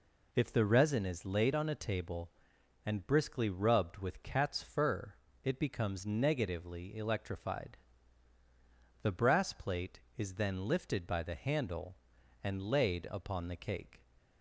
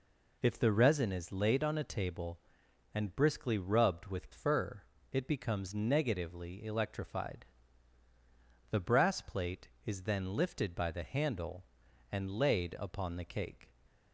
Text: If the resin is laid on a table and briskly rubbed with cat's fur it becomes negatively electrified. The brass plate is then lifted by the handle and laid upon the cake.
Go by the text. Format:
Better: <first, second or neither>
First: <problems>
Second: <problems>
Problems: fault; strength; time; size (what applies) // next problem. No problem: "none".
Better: first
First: pauses between "fur" and "it"; slight; at 5.1 s; 0.28 s long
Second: skips "cat's"; at 4.3 s // pauses between "fur" and "it"; slight; at 4.8 s; 0.28 s long